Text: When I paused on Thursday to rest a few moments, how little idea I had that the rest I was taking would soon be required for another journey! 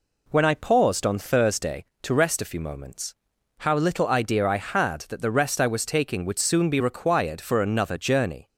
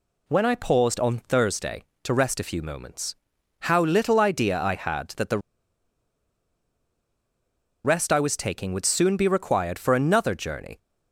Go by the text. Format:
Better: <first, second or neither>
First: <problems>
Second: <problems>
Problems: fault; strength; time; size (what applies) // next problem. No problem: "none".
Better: first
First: none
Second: pauses between "the" and "rest"; strong; at 5.3 s; 2.4 s long